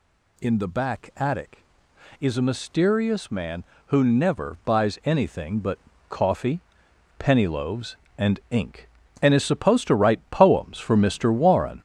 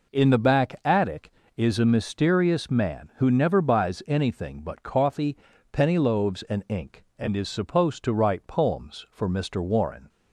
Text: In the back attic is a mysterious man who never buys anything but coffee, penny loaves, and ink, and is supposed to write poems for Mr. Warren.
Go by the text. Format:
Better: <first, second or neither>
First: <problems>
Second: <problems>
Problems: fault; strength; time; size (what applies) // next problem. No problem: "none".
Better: second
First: gets louder; noticeable; throughout; 5 dB // pauses between "but" and "coffee"; slight; at 5.7 s; 0.32 s long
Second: none